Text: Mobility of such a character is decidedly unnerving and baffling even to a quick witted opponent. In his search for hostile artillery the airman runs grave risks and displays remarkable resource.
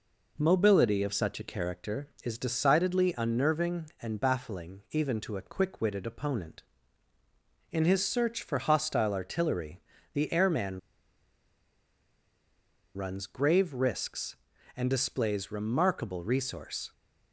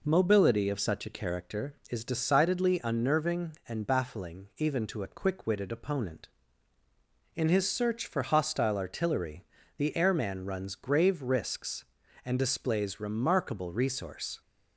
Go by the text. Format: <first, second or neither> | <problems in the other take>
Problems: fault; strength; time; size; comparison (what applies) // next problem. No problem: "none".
second | pauses between "artillery" and "the"; slight; at 9.8 s; 0.32 s long; slight in the second // pauses between "airman" and "runs"; strong; at 10.7 s; 2.1 s long